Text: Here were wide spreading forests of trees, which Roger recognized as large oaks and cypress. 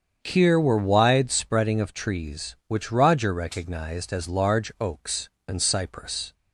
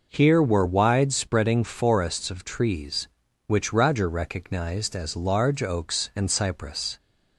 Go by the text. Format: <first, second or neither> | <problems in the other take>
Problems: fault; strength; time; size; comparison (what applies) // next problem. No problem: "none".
second | starts louder than the rest; strong; until 1.2 s; 7.5 dB // skips "forests"; at 1.8 s